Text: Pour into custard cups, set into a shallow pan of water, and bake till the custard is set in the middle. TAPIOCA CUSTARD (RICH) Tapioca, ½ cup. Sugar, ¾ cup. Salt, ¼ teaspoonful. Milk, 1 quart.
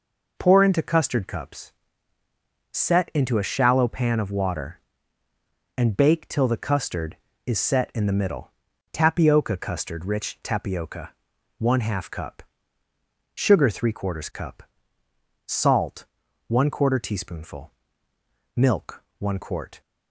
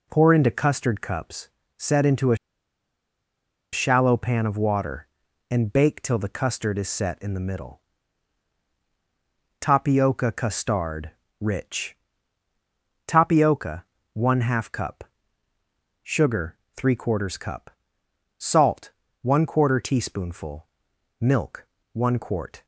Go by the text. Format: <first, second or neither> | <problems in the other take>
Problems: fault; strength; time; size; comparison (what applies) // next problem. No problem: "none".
first | pauses between "a" and "shallow"; strong; at 2.3 s; 1.3 s long